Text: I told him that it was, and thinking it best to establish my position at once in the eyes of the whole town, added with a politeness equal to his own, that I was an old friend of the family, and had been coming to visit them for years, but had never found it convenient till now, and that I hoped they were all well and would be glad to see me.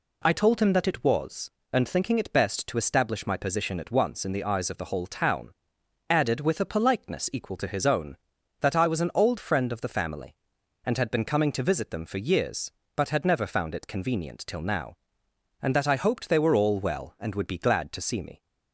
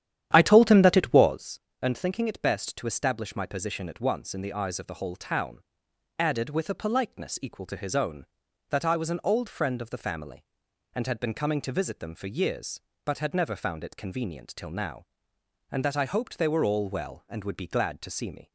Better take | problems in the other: first | starts louder than the rest; strong; until 1.5 s; 10.5 dB

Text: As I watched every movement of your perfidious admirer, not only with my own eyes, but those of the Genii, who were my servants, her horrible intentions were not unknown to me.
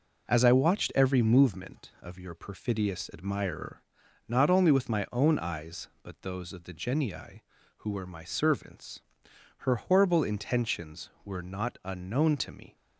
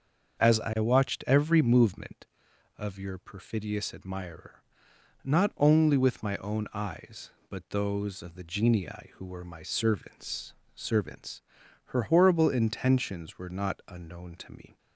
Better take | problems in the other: first | starts louder than the rest; until 1.4 s; 6.5 dB // says "servants" twice; at 10.7 s

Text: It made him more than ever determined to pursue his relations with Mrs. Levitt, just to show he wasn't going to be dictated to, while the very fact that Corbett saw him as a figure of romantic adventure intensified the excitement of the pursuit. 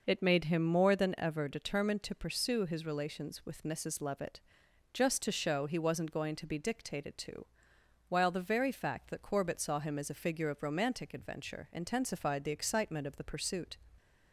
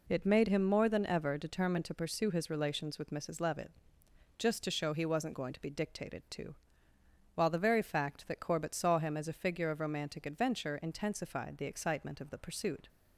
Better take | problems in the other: neither | none

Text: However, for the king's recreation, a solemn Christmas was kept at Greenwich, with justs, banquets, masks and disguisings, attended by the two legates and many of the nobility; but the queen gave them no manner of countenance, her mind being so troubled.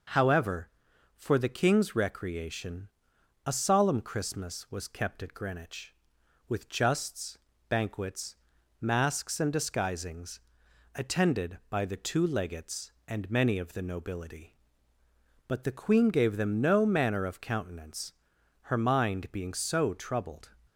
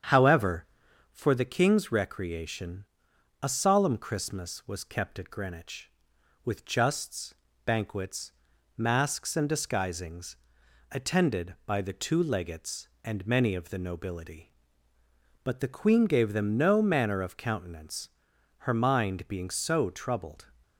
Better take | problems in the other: first | starts louder than the rest; strong; until 1.2 s; 8 dB

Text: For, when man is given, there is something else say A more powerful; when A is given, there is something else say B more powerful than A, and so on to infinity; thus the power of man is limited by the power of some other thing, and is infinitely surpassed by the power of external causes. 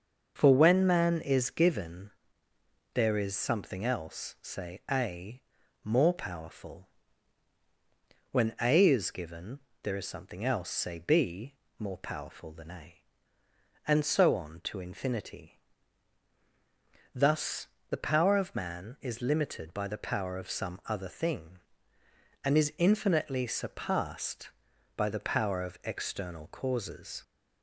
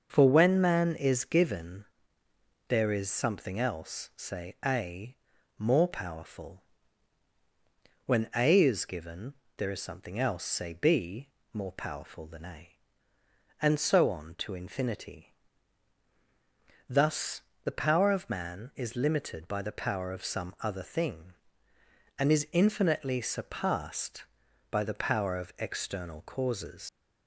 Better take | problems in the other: first | starts louder than the rest; until 1.1 s; 6.5 dB; also in the first // pauses between "A" and "more"; at 5.1 s; 0.42 s long; also in the first // pauses between "B" and "more"; slight; at 11.2 s; 0.24 s long; slight in the first // pauses between "thus" and "the"; slight; at 17.4 s; 0.22 s long; slight in the first // leaves "causes" unfinished; at 26.8 s; 80 ms

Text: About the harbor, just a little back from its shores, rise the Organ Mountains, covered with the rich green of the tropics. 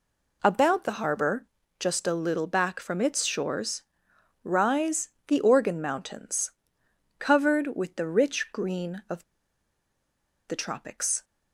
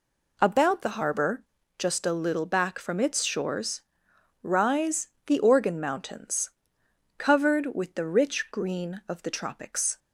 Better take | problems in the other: second | pauses between "rise" and "the"; slight; at 5.0 s; 0.18 s long; slight in the second // pauses between "of" and "the"; strong; at 9.2 s; 1.2 s long

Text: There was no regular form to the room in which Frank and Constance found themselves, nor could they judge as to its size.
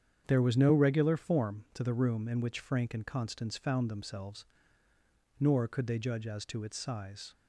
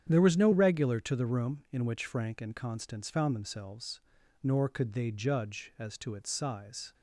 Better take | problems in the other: first | starts louder than the rest; strong; until 1.1 s; 9 dB; strong in the first // skips "form"; at 1.0 s

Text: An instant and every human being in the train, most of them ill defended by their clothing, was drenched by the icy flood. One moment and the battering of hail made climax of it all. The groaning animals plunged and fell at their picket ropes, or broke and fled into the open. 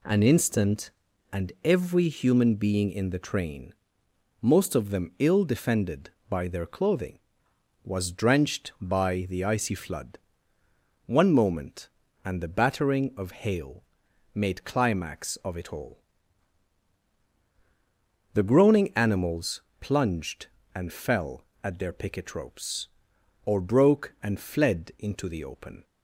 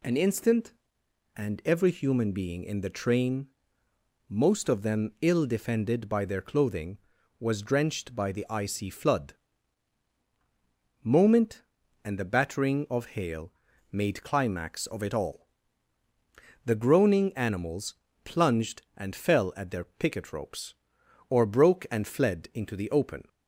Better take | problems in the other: first | skips "One"; at 10.1 s // pauses between "hail" and "made"; at 13.5 s; 0.40 s long; noticeable in the first // pauses between "animals" and "plunged"; slight; at 17.9 s; 0.30 s long; slight in the first

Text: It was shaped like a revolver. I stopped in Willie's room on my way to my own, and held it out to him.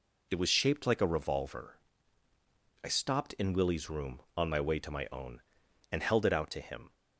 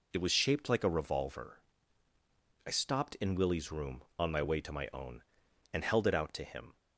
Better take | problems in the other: neither | none

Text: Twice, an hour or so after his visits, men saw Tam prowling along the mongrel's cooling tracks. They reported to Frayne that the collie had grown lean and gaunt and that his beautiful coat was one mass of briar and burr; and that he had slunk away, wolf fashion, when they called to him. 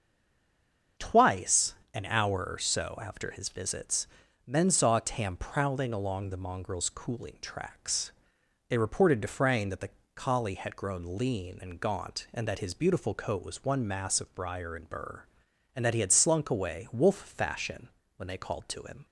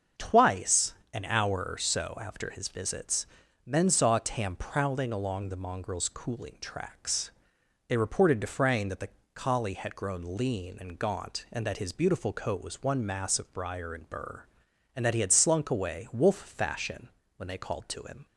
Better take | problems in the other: second | stays silent before the first word; until 0.9 s; 0.9 s long // starts louder than the rest; until 2.1 s; 6.5 dB; also in the second // pauses between "the" and "collie"; slight; at 9.9 s; 0.24 s long; slight in the second

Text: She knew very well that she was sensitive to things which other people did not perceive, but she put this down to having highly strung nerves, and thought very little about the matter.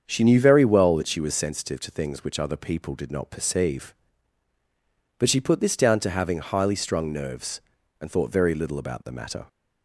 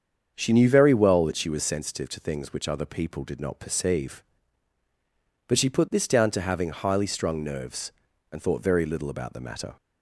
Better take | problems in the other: neither | starts louder than the rest; strong; the same in both

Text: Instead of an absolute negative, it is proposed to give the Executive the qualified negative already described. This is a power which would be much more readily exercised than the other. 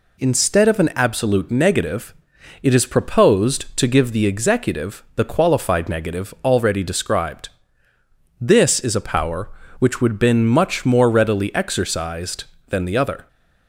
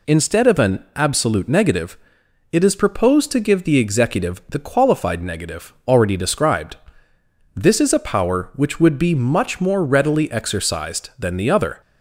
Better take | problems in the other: second | says "been" for "be"; at 10.1 s

